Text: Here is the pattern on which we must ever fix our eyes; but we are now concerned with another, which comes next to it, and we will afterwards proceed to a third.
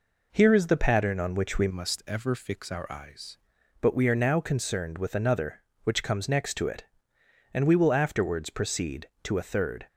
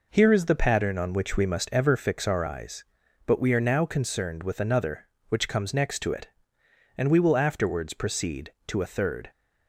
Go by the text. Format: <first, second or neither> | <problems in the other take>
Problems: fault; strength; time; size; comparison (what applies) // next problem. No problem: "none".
second | changes voice from "must" to "eyes"; from 1.6 to 3.3 s; 1.7 s long